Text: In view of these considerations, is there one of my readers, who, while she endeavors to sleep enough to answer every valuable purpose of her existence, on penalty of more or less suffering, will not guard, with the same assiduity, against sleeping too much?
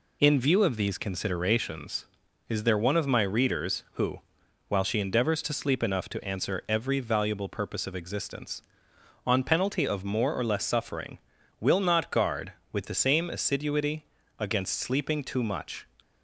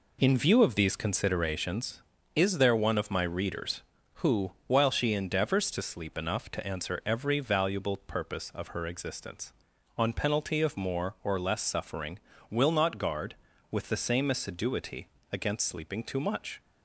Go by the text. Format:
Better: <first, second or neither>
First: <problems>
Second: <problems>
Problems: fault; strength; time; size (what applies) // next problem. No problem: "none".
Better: second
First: skips "her"; at 7.9 s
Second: none